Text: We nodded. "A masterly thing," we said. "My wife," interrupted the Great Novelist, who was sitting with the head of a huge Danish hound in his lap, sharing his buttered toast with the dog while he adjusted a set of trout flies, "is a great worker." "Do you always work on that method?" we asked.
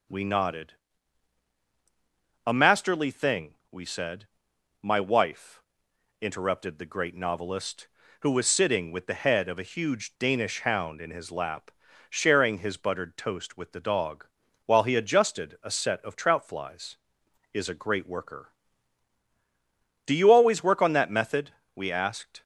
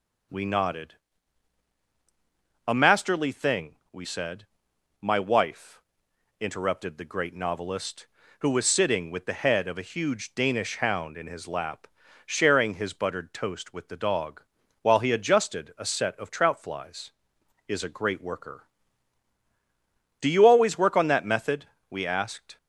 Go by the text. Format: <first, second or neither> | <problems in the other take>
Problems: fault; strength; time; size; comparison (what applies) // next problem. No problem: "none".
neither | starts louder than the rest; noticeable; the same in both // pauses between "dog" and "while"; the same in both